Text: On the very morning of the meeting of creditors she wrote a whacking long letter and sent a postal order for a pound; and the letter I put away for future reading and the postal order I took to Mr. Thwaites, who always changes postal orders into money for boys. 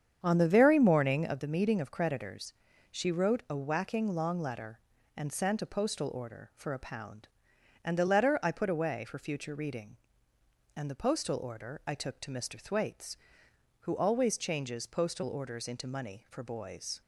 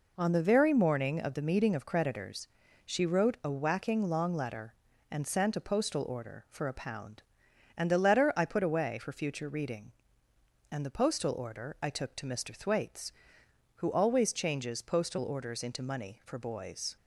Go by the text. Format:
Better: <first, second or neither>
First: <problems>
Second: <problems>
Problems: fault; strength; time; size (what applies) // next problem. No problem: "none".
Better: second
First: starts louder than the rest; strong; until 1.4 s; 8 dB // pauses between "creditors" and "she"; at 2.5 s; 0.38 s long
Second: pauses between "creditors" and "she"; at 2.4 s; 0.38 s long